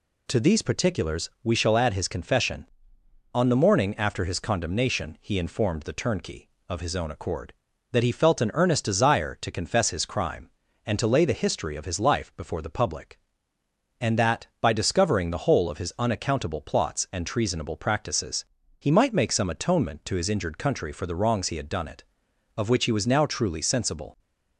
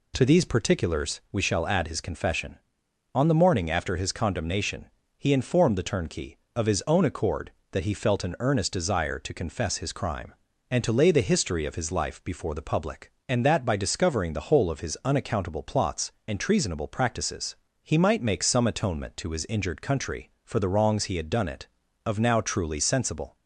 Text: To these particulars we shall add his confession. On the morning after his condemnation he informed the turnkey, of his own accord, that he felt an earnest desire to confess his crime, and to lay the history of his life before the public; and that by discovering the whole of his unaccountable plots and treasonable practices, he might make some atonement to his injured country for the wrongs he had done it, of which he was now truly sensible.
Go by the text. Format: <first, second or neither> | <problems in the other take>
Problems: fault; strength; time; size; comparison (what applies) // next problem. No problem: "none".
first | pauses between "condemnation" and "he"; slight; at 4.8 s; 0.34 s long // skips "which he was"; at 22.2 s